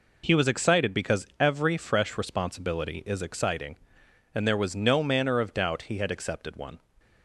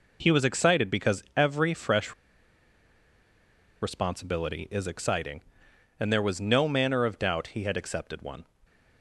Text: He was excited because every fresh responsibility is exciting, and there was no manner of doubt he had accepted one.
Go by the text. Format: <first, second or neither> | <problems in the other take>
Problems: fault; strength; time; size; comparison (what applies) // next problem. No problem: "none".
first | pauses between "fresh" and "responsibility"; strong; at 2.1 s; 1.6 s long // stays silent after the last word; slight; from 8.4 s on; 0.6 s long